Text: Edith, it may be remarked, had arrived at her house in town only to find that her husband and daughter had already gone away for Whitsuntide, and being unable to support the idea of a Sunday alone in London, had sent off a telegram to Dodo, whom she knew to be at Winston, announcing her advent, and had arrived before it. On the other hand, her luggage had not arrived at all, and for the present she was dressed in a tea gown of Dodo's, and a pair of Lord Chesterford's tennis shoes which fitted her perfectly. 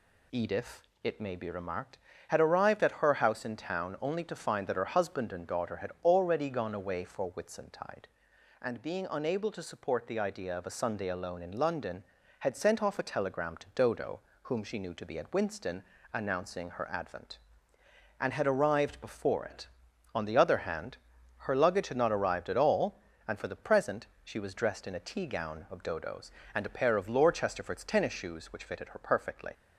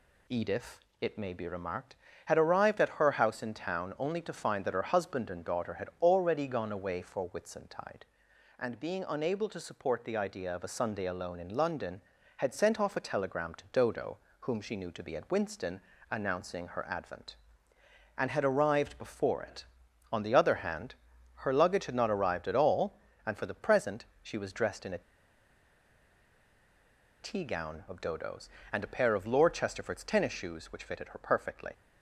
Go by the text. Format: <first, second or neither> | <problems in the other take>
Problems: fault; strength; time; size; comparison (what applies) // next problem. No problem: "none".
first | pauses between "present" and "she"; slight; at 24.0 s; 0.18 s long; slight in the first // pauses between "a" and "tea"; strong; at 25.0 s; 2.2 s long